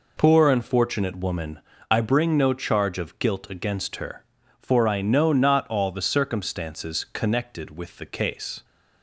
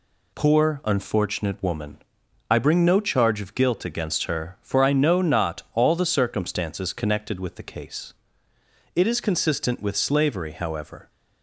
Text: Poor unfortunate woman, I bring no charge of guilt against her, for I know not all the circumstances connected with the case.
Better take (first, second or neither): first